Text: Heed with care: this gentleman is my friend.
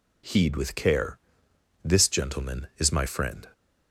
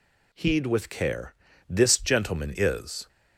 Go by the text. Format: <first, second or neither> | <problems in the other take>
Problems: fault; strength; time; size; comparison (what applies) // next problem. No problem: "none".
first | stops before "my friend"; at 3.0 s